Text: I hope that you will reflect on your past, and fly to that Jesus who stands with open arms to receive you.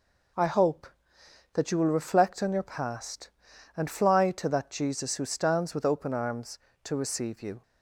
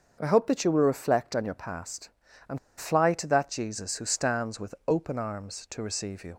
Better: first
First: none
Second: starts louder than the rest; until 1.2 s; 6.5 dB // pauses between "and" and "fly"; slight; at 2.5 s; 0.19 s long

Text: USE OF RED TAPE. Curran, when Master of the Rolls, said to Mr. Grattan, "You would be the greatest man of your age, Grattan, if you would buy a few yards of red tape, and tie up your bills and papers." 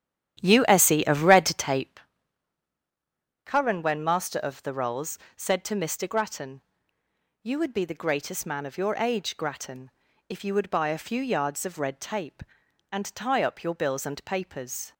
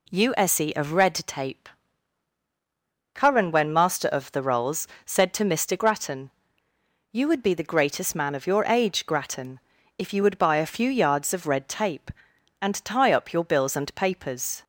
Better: second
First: starts louder than the rest; strong; until 2.0 s; 11 dB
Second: none

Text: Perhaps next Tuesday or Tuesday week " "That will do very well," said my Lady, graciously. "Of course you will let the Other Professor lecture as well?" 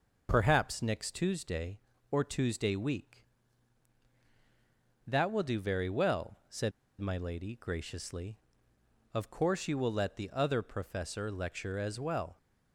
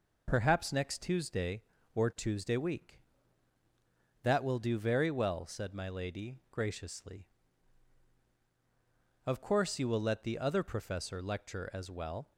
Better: second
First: pauses between "said" and "my"; slight; at 6.7 s; 0.27 s long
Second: none

